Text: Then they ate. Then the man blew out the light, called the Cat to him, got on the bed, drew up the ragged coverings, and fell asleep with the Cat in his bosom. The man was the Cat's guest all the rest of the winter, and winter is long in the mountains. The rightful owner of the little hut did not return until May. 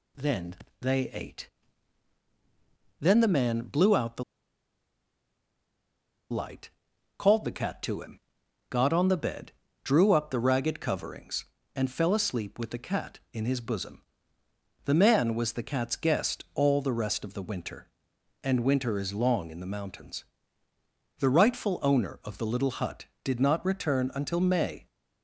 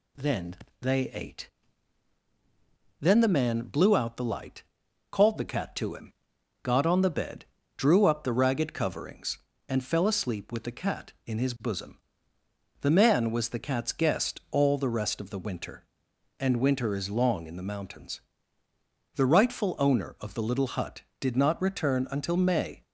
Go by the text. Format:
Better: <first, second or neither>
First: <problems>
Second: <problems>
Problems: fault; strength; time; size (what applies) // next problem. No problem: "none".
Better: second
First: pauses between "Then" and "they"; slight; at 0.5 s; 0.24 s long // pauses between "the" and "light"; strong; at 4.2 s; 2.0 s long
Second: pauses between "Then" and "they"; slight; at 0.5 s; 0.24 s long